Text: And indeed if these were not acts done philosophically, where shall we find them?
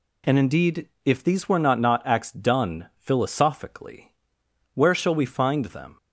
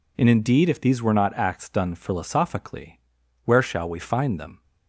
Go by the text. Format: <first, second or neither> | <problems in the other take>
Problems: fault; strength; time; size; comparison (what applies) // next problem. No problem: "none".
second | pauses between "indeed" and "if"; slight; at 0.8 s; 0.16 s long // says "not" twice; at 1.7 s